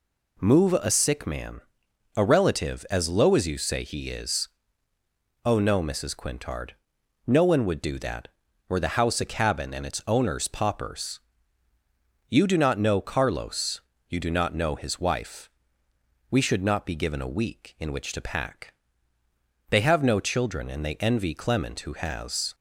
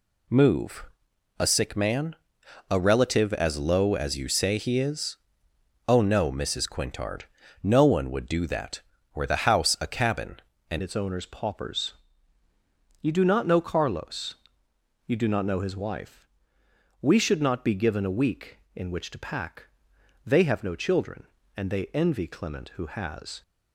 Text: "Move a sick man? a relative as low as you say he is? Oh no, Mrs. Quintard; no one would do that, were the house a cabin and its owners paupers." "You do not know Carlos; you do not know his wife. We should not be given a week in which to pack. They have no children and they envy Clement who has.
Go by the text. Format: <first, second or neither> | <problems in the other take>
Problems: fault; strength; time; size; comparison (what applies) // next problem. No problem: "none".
first | pauses between "Move" and "a"; noticeable; at 0.8 s; 0.50 s long // changes voice at "its"; from 10.8 s on; 12.6 s long